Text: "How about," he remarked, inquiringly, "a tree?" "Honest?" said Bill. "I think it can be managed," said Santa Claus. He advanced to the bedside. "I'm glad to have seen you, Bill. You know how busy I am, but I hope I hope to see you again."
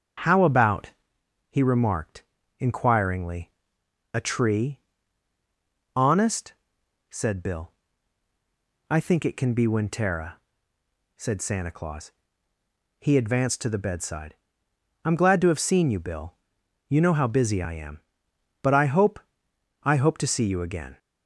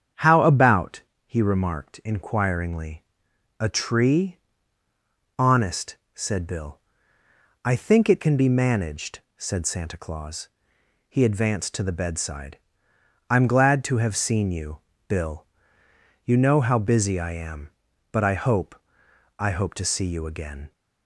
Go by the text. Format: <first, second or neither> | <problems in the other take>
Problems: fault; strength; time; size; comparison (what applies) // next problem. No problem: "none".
second | starts louder than the rest; until 1.8 s; 7 dB; strong in the second // says "wintera" for "managed"; at 9.6 s // pauses between "hope" and "I"; noticeable; at 19.1 s; 0.64 s long; noticeable in the second